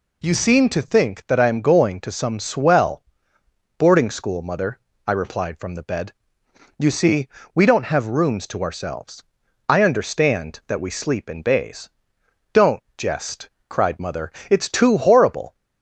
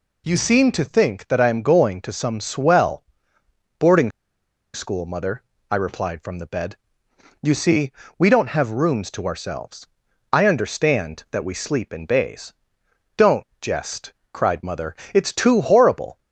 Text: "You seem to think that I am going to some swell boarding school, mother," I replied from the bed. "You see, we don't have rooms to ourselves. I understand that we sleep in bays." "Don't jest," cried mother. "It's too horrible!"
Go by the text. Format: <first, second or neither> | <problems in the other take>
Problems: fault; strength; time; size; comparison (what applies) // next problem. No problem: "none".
first | pauses between "swell" and "boarding"; noticeable; at 3.0 s; 0.74 s long; noticeable in the first // pauses between "boarding" and "school"; noticeable; at 4.0 s; 0.63 s long // pauses between "Don't" and "jest"; slight; at 13.4 s; 0.16 s long; slight in the first